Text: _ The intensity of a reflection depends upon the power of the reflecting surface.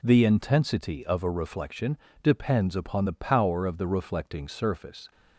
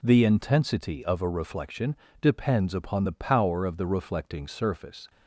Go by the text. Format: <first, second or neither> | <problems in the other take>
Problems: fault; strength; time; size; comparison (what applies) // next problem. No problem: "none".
neither | pauses between "reflection" and "depends"; slight; the same in both